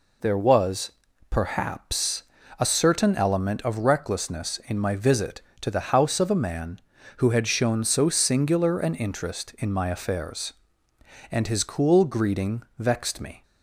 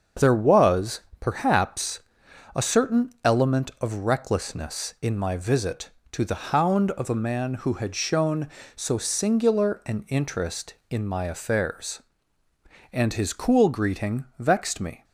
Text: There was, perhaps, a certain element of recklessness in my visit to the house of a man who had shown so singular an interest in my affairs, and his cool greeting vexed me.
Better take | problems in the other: first | starts louder than the rest; until 1.3 s; 6.5 dB // says "hound" for "house"; at 6.4 s // pauses between "greeting" and "vexed"; slight; at 14.2 s; 0.16 s long; slight in the first

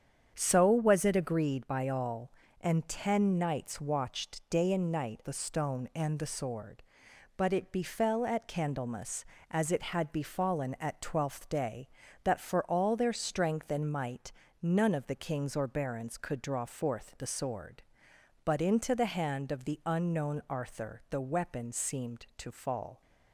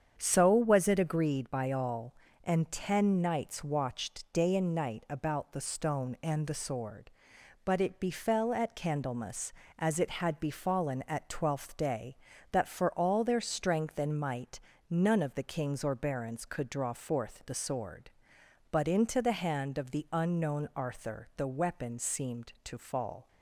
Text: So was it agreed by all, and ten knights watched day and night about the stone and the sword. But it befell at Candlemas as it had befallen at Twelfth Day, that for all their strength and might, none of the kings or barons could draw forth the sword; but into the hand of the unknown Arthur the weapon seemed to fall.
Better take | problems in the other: second | starts louder than the rest; strong; until 1.3 s; 8 dB; strong in the second // skips "about"; at 5.2 s

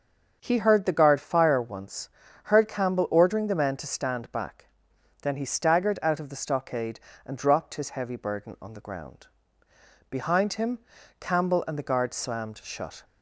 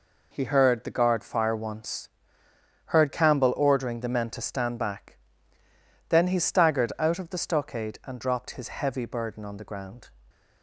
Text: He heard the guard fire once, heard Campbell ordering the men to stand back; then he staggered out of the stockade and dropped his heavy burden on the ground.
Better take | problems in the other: second | starts louder than the rest; until 1.4 s; 6.5 dB // goes on to say "Behind him Campbell and the guard slammed shut"; strong; from 10.0 s on; 2.9 s long

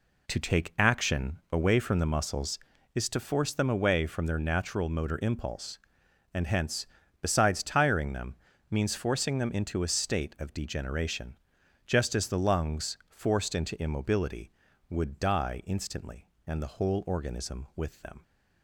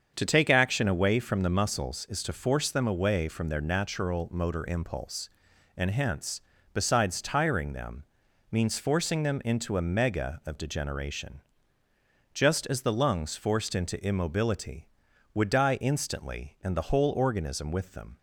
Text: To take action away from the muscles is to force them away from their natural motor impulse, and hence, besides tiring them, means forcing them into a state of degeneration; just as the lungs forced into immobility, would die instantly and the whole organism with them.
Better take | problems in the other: first | starts louder than the rest; strong; until 1.1 s; 7 dB // says "mega" for "state"; at 9.8 s

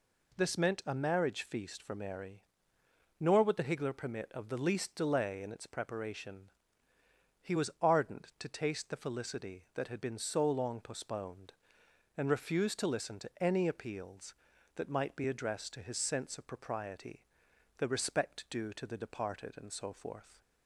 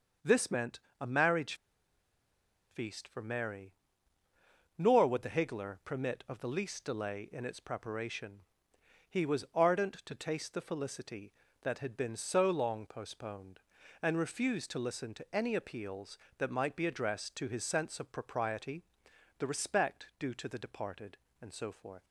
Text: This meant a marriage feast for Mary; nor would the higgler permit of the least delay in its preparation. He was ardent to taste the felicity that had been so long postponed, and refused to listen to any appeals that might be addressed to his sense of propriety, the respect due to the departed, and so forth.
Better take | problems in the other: first | starts louder than the rest; until 1.4 s; 6.5 dB // pauses between "meant" and "a"; slight; at 0.7 s; 0.20 s long // pauses between "marriage" and "feast"; at 1.5 s; 1.1 s long

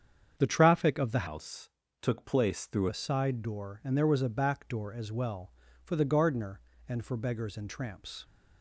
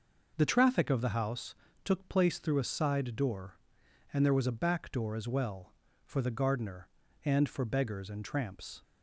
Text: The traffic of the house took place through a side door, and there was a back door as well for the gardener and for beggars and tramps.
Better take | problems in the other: second | starts louder than the rest; strong; until 1.3 s; 7.5 dB // changes voice from "house" to "through"; from 1.2 to 2.8 s; 1.6 s long // pauses between "house" and "took"; slight; at 1.6 s; 0.32 s long; slight in the second

